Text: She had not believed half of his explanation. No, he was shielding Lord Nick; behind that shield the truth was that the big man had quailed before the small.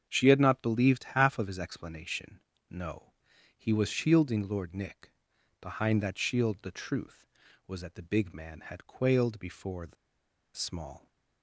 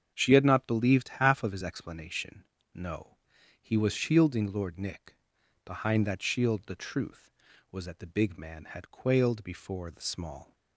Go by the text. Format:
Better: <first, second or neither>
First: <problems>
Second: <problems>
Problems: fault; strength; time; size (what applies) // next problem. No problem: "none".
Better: second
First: starts louder than the rest; strong; until 1.1 s; 7.5 dB // pauses between "the" and "small"; noticeable; at 9.9 s; 0.60 s long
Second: starts louder than the rest; until 1.1 s; 7 dB